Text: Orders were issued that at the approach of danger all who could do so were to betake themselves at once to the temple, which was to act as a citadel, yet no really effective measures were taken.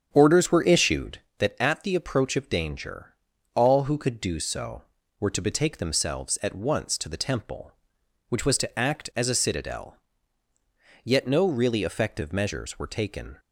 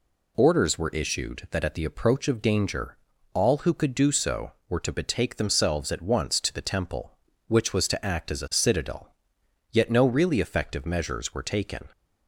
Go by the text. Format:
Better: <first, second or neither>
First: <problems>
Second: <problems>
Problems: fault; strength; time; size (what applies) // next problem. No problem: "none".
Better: second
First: starts louder than the rest; strong; until 1.4 s; 8 dB // pauses between "danger" and "all"; at 3.1 s; 0.40 s long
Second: pauses between "danger" and "all"; slight; at 2.9 s; 0.36 s long